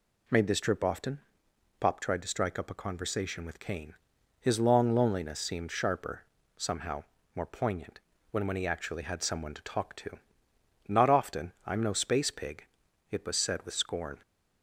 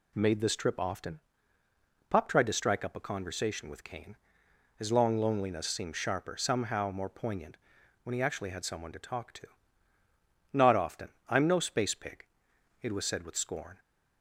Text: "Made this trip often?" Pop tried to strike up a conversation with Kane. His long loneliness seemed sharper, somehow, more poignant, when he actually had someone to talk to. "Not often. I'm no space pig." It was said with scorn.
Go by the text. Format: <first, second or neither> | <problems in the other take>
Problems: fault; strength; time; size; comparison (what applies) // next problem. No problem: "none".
second | says "when" twice; at 8.4 s